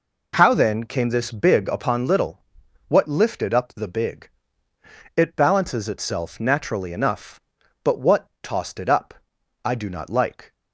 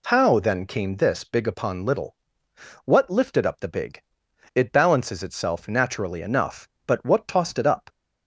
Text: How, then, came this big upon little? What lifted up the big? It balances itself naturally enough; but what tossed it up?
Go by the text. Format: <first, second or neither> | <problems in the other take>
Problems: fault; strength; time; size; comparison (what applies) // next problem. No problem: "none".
second | goes on to say "I do not like"; noticeable; from 9.6 s on; 0.88 s long